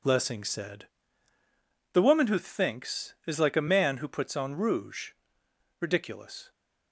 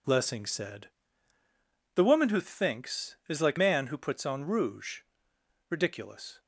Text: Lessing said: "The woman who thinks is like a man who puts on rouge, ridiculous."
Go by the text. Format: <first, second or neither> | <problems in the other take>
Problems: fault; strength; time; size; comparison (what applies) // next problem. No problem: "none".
first | skips "a"; at 3.5 s